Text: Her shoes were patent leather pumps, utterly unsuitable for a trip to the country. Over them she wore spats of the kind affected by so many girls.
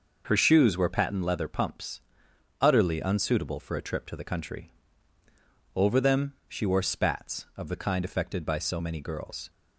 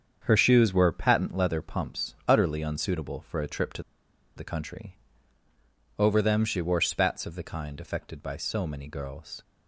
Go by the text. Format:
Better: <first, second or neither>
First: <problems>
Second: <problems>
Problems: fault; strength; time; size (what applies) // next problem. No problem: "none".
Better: first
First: none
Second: starts louder than the rest; strong; until 1.2 s; 7.5 dB // pauses between "to" and "the"; noticeable; at 3.8 s; 0.53 s long